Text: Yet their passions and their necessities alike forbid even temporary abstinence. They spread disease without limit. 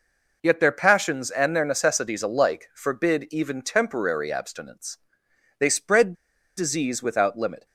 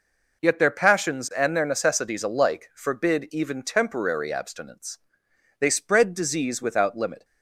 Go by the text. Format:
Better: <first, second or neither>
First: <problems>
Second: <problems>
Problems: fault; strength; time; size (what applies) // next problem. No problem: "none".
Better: second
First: pauses between "spread" and "disease"; at 6.1 s; 0.43 s long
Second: none